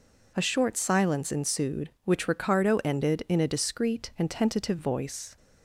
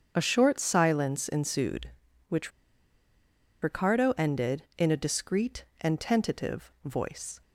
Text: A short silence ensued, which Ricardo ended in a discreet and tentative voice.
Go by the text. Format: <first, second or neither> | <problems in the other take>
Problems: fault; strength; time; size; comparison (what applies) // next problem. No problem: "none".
first | starts louder than the rest; strong; until 1.1 s; 7.5 dB // pauses between "which" and "Ricardo"; at 2.5 s; 1.1 s long